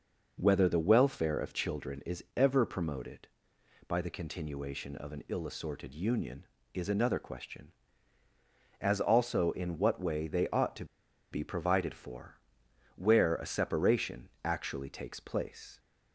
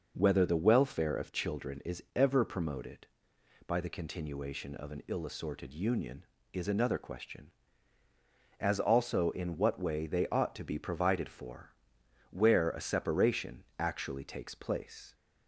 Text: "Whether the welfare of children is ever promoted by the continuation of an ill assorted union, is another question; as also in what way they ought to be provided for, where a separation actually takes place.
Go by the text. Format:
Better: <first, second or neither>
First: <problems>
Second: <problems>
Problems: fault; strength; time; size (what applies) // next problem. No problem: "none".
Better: second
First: pauses between "to" and "be"; noticeable; at 10.8 s; 0.46 s long // pauses between "separation" and "actually"; slight; at 14.2 s; 0.16 s long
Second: pauses between "separation" and "actually"; slight; at 13.6 s; 0.16 s long